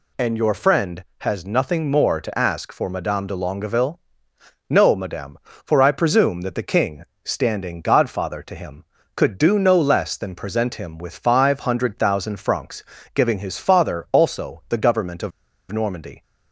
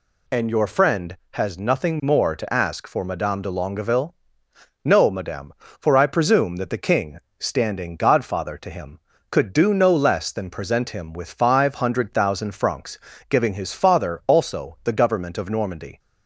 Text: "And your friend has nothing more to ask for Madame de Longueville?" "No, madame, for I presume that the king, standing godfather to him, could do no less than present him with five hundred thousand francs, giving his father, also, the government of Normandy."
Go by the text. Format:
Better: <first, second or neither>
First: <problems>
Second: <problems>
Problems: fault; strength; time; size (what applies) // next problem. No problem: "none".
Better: second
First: pauses between "of" and "Normandy"; at 15.3 s; 0.40 s long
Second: none